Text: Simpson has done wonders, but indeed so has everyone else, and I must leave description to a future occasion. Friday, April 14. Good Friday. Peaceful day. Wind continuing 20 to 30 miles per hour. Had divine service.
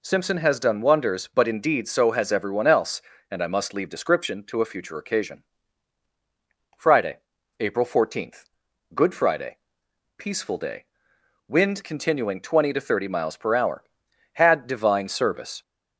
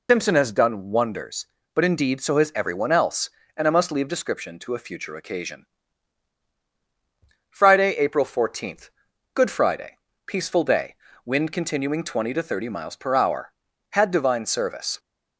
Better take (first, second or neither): first